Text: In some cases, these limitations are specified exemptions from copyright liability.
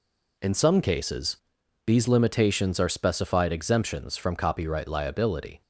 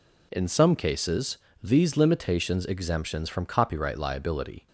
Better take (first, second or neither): first